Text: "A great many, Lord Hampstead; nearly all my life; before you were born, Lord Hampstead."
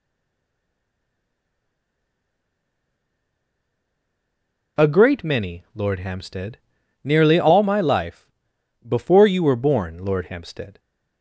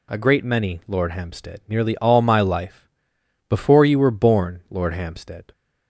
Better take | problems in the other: second | stays silent before the first word; strong; until 4.7 s; 4.7 s long

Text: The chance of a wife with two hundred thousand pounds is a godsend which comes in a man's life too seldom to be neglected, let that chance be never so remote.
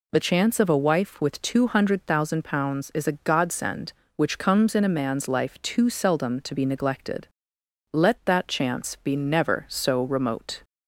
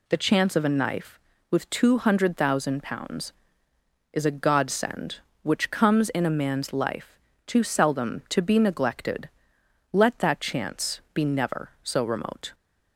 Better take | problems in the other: first | says "knife" for "wife"; at 0.6 s // pauses between "life" and "too"; slight; at 7.1 s; 0.28 s long

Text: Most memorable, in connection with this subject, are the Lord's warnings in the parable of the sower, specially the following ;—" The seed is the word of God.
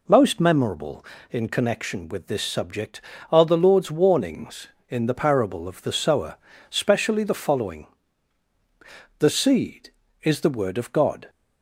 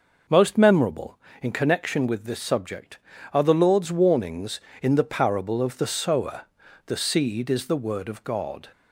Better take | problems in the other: first | skips "specially the following"; at 6.5 s

